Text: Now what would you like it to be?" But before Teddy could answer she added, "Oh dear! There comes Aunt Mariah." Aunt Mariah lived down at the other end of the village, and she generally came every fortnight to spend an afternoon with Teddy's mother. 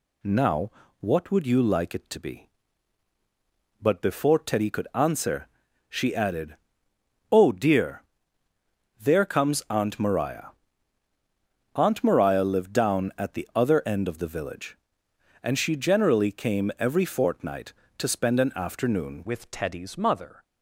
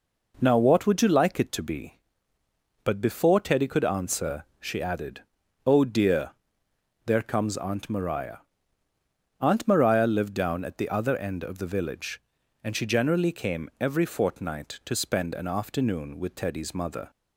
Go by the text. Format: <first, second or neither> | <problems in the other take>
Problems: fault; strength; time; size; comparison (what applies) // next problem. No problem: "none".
second | pauses between "Now" and "what"; slight; at 0.6 s; 0.30 s long // pauses between "answer" and "she"; at 5.4 s; 0.40 s long; slight in the second // changes voice at "with"; from 19.2 s on; 1.2 s long